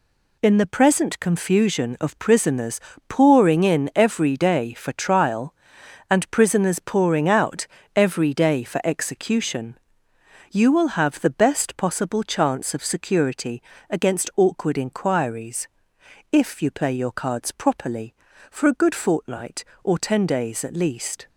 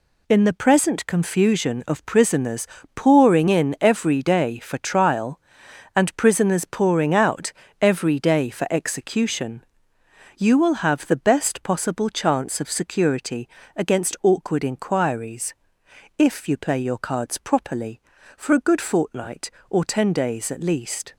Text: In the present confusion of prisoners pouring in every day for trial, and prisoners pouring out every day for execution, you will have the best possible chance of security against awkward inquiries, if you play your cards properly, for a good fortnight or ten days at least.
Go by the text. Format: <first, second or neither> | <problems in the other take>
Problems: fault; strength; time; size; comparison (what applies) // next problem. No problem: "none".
neither | pauses between "prisoners" and "pouring"; slight; the same in both // pauses between "out" and "every"; slight; the same in both // pauses between "security" and "against"; slight; the same in both